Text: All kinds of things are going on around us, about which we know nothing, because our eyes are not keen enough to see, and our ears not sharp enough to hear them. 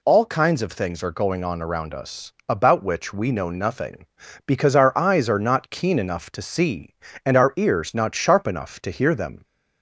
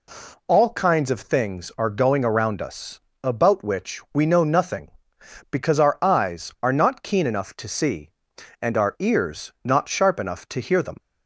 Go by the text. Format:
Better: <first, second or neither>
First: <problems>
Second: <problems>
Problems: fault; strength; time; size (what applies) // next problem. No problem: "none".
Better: first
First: none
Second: skips "on"; at 2.2 s